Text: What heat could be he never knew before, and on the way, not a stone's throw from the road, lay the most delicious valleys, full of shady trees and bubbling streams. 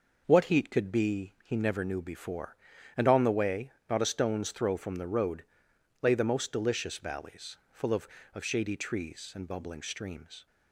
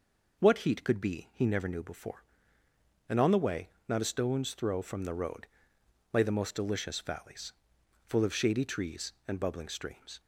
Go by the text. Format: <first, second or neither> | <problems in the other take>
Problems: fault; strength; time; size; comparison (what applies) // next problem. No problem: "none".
second | says "of" twice; at 8.3 s